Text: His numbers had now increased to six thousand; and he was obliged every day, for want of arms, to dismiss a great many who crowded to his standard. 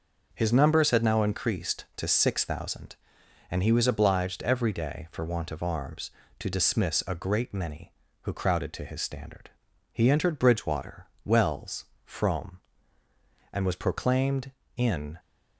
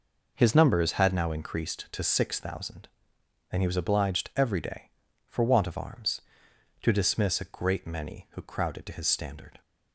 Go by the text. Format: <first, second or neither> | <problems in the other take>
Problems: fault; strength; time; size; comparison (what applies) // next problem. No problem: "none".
second | goes on to say "He entered Bridgewater Wells Frome and was proclaimed in"; strong; from 9.9 s on; 5.2 s long